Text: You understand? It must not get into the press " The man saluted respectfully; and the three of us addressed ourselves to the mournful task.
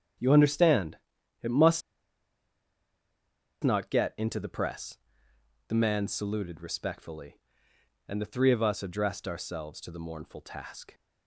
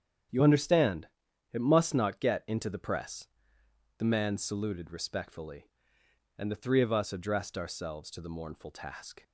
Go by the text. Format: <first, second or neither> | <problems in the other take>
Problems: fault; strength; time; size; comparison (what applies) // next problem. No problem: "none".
second | starts louder than the rest; strong; until 1.6 s; 9.5 dB; strong in the second // pauses between "must" and "not"; strong; at 1.8 s; 1.8 s long